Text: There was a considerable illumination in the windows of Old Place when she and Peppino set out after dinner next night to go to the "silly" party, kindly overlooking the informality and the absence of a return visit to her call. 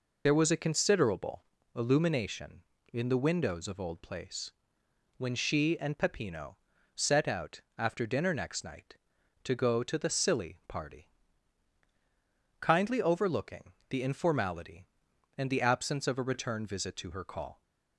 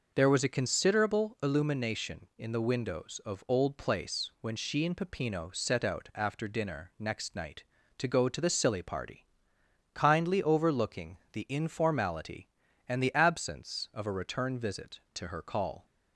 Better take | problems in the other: second | loses the start of "There"; at 0.2 s; 30 ms // pauses between "considerable" and "illumination"; slight; at 1.4 s; 0.30 s long // pauses between "Place" and "when"; noticeable; at 4.5 s; 0.64 s long // pauses between "Peppino" and "set"; slight; at 6.5 s; 0.36 s long // pauses between "out" and "after"; slight; at 7.6 s; 0.16 s long // pauses between "overlooking" and "the"; slight; at 13.7 s; 0.16 s long

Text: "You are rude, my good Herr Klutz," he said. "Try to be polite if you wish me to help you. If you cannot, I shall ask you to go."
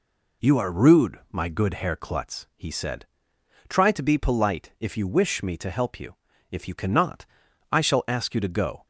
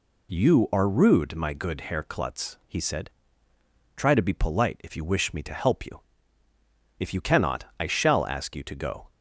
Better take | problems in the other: neither | none

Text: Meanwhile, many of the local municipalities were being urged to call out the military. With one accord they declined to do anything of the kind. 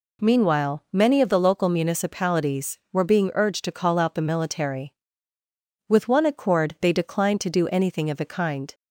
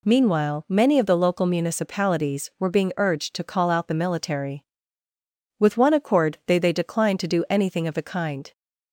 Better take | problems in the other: first | says "they" twice; at 6.5 s

